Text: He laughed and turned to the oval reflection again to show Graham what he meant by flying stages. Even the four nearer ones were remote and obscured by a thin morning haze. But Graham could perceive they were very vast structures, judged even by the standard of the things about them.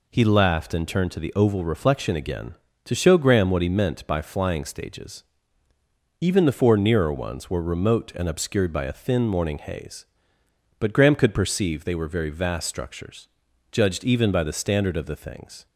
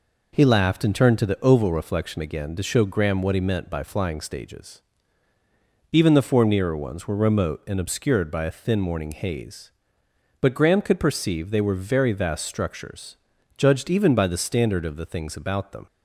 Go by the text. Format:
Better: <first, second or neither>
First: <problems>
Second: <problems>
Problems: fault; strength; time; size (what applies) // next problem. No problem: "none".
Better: second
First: stops before "about them"; at 15.6 s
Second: none